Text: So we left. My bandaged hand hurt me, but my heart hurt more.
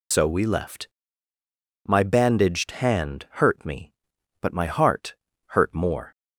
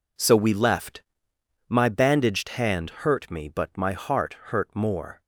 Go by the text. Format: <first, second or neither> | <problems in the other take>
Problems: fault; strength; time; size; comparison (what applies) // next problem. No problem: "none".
second | loses the start of "So"; at 0.1 s; 65 ms // pauses between "heart" and "hurt"; slight; at 5.1 s; 0.34 s long